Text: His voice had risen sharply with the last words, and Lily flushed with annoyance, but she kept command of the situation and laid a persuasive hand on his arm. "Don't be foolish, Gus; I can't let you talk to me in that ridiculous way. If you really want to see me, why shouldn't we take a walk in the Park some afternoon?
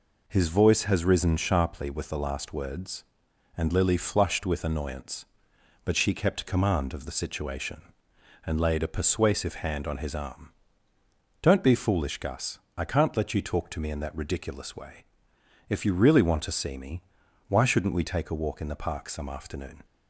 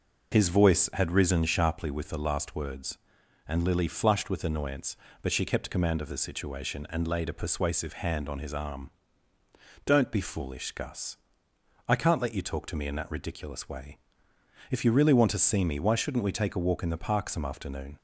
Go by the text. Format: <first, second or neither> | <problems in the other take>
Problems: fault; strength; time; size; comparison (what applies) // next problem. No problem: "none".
second | says "has" for "had"; at 0.8 s